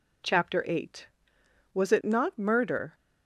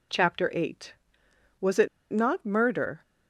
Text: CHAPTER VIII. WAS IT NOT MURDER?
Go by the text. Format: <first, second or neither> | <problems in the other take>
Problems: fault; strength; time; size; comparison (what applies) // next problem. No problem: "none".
first | pauses between "IT" and "NOT"; slight; at 1.8 s; 0.25 s long